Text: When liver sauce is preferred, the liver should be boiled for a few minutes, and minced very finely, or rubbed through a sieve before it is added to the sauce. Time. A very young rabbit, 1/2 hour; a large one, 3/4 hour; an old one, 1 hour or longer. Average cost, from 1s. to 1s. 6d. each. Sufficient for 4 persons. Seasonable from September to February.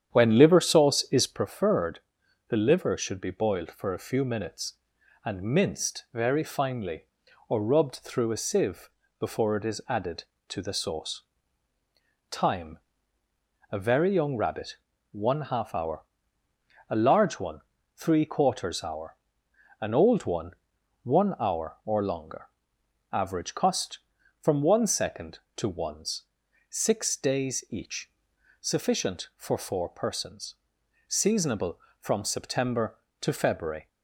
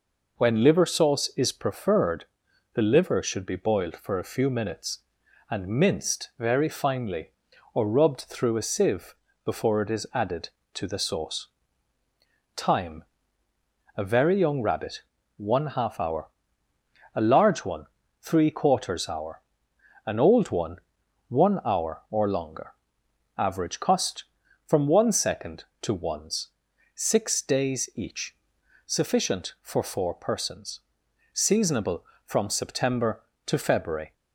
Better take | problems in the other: second | starts louder than the rest; strong; until 1.5 s; 9 dB // pauses between "sieve" and "before"; slight; at 8.8 s; 0.30 s long; slight in the second

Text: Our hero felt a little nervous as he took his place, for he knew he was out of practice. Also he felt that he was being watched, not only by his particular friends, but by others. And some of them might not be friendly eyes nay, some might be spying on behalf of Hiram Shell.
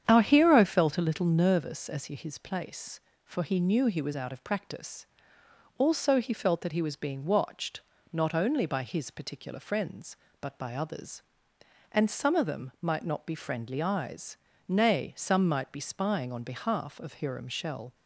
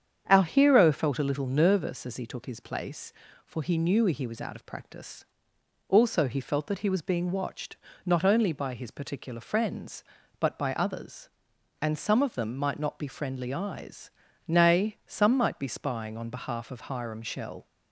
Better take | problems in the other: second | starts louder than the rest; strong; until 1.0 s; 8.5 dB; strong in the second // skips "took"; at 2.1 s // pauses between "eyes" and "nay"; slight; at 14.3 s; 0.30 s long; slight in the second

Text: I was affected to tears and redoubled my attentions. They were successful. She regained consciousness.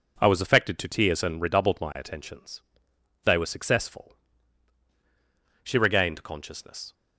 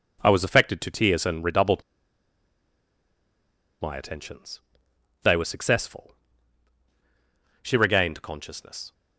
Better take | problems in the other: first | pauses between "redoubled" and "my"; strong; at 1.8 s; 1.9 s long

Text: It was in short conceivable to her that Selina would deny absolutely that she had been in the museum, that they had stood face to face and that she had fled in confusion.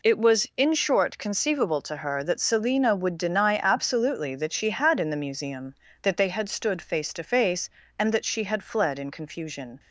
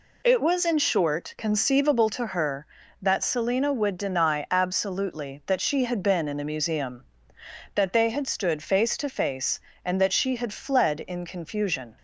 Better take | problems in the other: second | skips "been"; at 4.9 s

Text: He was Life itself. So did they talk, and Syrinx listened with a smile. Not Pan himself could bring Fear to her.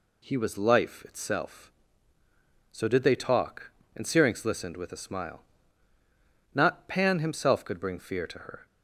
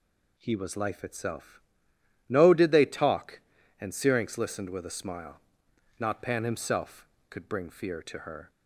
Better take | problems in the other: first | says "No" for "So"; at 2.2 s

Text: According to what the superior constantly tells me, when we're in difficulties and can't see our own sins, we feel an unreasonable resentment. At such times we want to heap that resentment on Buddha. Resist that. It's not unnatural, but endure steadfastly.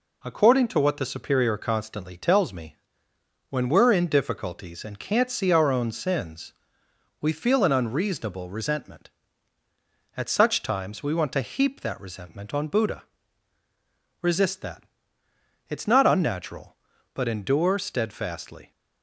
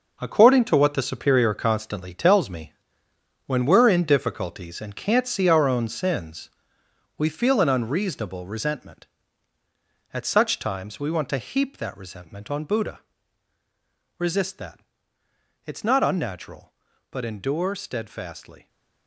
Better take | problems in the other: first | gets quieter; strong; throughout; 9.5 dB

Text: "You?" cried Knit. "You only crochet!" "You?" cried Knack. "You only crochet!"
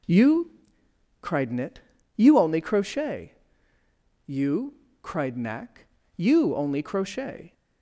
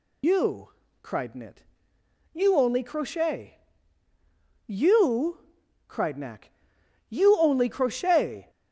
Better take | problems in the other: first | loses the start of "You"; at 0.2 s; 100 ms

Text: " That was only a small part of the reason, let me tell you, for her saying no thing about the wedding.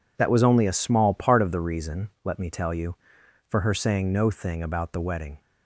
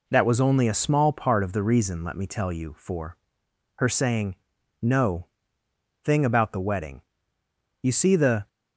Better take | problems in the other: first | pauses between "for" and "her"; noticeable; at 3.1 s; 0.58 s long // pauses between "saying" and "no"; noticeable; at 4.3 s; 0.46 s long // pauses between "no" and "thing"; noticeable; at 5.2 s; 0.78 s long // goes on to say "You see the"; noticeable; from 7.8 s on; 0.66 s long

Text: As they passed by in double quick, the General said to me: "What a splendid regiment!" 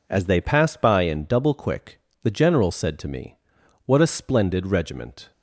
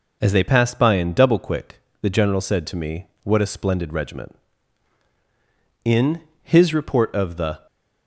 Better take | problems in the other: first | goes on to say "In his report of the"; strong; from 5.8 s on; 1.8 s long

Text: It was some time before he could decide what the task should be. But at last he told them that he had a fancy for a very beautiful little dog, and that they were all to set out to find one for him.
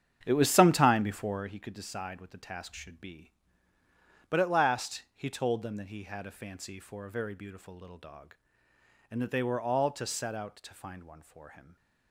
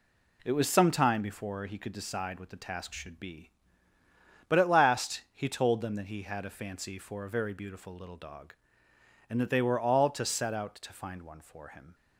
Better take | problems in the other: second | starts louder than the rest; strong; until 1.5 s; 8.5 dB

